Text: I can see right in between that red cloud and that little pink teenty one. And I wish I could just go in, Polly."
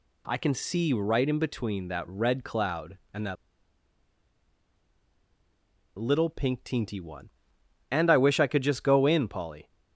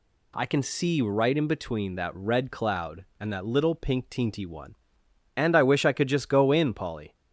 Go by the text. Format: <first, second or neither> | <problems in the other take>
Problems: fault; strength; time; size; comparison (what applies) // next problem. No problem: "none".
second | pauses between "that" and "little"; strong; at 3.3 s; 2.6 s long